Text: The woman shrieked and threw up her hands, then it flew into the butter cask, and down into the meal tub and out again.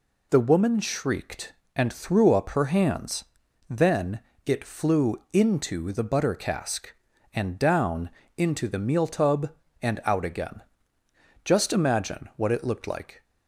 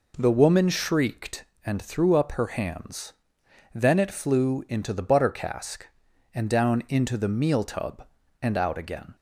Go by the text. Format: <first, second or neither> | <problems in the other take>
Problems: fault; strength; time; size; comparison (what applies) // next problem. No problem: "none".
second | pauses between "then" and "it"; slight; at 4.2 s; 0.22 s long // pauses between "down" and "into"; slight; at 8.0 s; 0.26 s long // goes on to say "Just imagine what it looked like"; strong; from 11.4 s on; 1.8 s long